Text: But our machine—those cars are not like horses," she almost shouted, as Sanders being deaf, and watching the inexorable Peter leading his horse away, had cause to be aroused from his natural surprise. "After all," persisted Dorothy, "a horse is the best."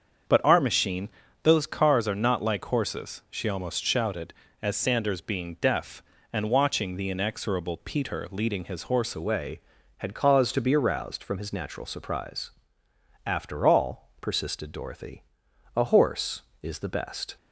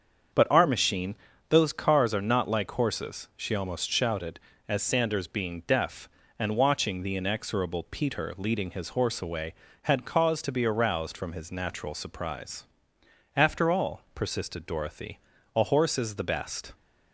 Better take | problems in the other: second | starts louder than the rest; until 1.6 s; 7 dB; also in the second // changes voice at "away"; from 9.1 s on; 8.2 s long

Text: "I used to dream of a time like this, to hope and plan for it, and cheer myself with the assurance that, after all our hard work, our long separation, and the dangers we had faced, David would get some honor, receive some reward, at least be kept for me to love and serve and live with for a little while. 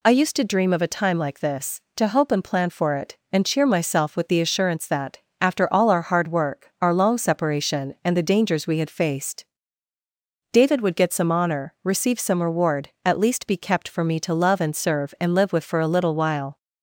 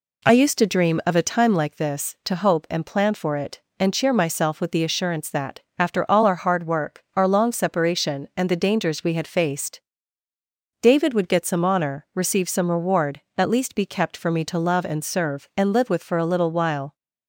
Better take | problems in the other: first | starts louder than the rest; slight; until 1.8 s; 3 dB

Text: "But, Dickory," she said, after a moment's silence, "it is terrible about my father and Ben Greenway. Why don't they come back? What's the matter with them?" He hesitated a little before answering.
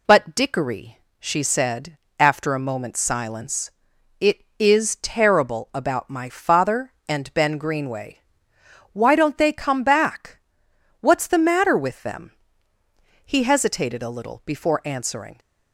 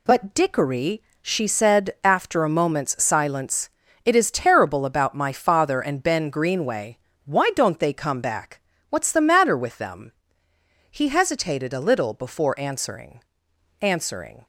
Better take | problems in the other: first | says "answering" twice; at 13.8 s

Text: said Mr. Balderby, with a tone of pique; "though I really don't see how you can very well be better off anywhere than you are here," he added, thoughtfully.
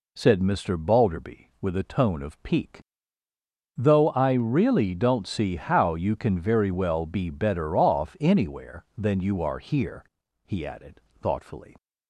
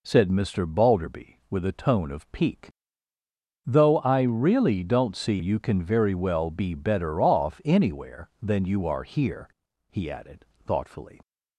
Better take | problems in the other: first | skips "how"; at 5.3 s

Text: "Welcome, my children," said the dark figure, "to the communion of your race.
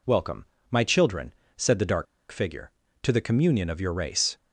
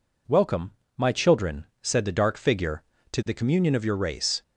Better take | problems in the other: second | pauses between "dark" and "figure"; slight; at 2.0 s; 0.25 s long

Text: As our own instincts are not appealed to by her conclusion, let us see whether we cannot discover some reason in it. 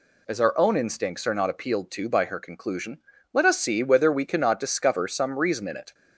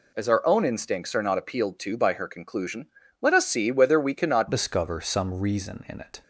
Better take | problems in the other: first | changes voice at "discover"; from 4.5 s on; 1.7 s long

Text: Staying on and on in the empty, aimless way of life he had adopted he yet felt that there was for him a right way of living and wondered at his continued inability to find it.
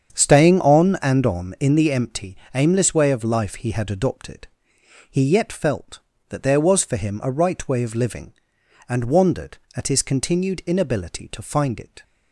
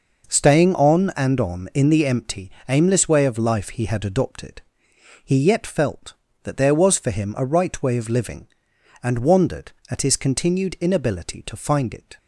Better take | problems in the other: second | starts louder than the rest; strong; until 1.5 s; 7.5 dB // pauses between "adopted" and "he"; noticeable; at 4.4 s; 0.66 s long; noticeable in the second

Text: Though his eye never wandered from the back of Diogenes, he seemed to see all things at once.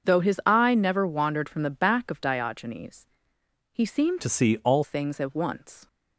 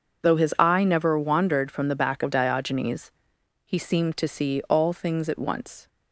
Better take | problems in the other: second | starts louder than the rest; until 1.1 s; 7 dB // changes voice from "to" to "all"; from 4.2 to 4.8 s; 0.6 s long

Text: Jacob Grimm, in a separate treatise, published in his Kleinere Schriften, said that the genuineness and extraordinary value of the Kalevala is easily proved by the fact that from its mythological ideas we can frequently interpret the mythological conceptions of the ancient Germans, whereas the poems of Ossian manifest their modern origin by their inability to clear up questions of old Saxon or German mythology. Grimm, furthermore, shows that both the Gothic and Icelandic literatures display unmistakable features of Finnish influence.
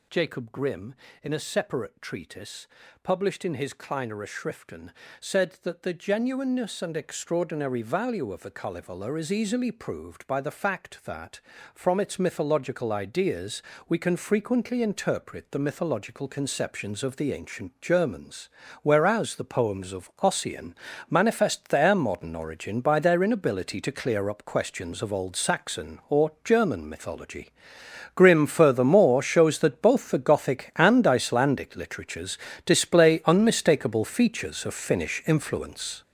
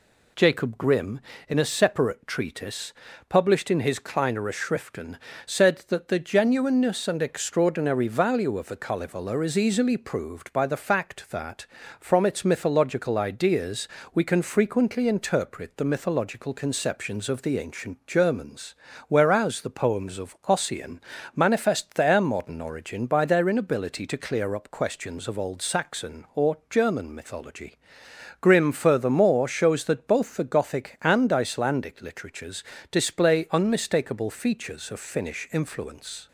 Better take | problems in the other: second | gets louder; strong; throughout; 9 dB // pauses between "ideas" and "we"; slight; at 13.6 s; 0.26 s long; slight in the second // pauses between "Ossian" and "manifest"; slight; at 20.7 s; 0.34 s long; slight in the second // pauses between "literatures" and "display"; slight; at 32.3 s; 0.28 s long; slight in the second

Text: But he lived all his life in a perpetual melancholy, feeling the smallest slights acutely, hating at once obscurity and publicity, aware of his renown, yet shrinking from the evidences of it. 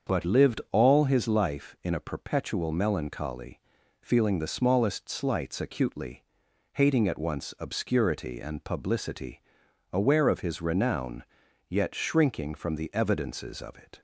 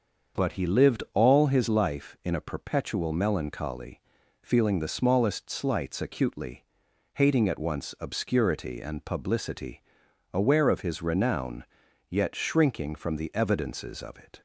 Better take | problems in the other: second | starts louder than the rest; until 1.2 s; 7 dB; also in the second // skips "he"; at 0.2 s

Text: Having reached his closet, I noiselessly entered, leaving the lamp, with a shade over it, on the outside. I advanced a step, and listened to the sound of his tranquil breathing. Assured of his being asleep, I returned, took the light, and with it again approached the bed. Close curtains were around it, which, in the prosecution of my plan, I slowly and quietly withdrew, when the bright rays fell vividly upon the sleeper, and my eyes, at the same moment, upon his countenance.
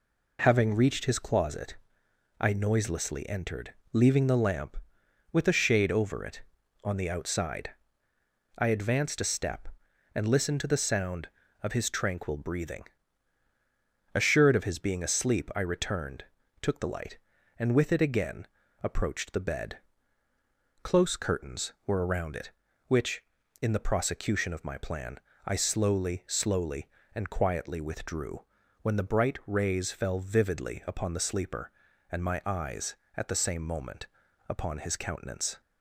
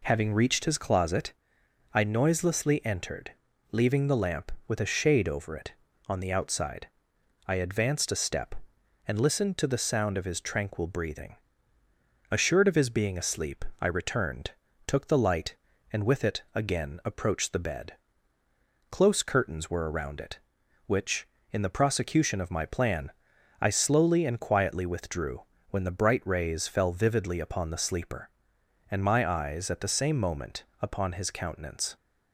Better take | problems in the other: second | pauses between "again" and "approached"; slight; at 18.4 s; 0.36 s long // says "slowly" twice; at 26.2 s

